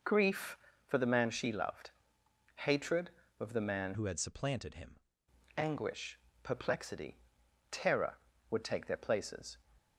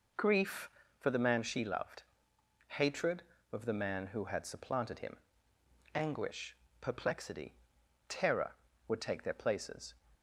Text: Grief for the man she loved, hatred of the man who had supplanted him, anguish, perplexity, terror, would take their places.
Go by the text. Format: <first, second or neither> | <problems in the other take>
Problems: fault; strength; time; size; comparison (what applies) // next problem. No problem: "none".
second | changes voice from "who" to "him"; from 3.9 to 4.9 s; 1.0 s long